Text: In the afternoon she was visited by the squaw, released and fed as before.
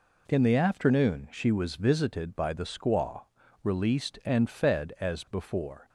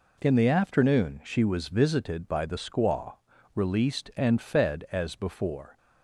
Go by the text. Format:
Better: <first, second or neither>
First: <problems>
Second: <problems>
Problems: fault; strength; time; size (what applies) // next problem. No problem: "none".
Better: neither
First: none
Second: none